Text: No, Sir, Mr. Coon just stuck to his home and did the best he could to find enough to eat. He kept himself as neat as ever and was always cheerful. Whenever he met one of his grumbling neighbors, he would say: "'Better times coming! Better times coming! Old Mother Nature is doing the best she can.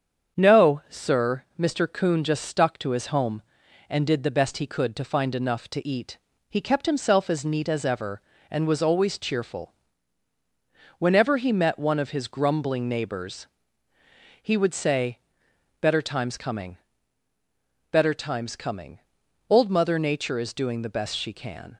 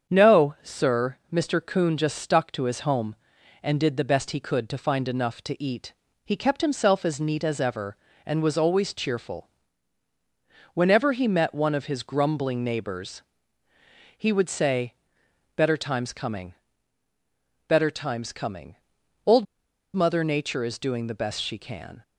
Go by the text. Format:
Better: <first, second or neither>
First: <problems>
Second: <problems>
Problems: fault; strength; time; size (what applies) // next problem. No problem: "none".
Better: first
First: starts louder than the rest; strong; until 1.4 s; 7.5 dB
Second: starts louder than the rest; strong; until 1.1 s; 7.5 dB // pauses between "Old" and "Mother"; noticeable; at 19.4 s; 0.50 s long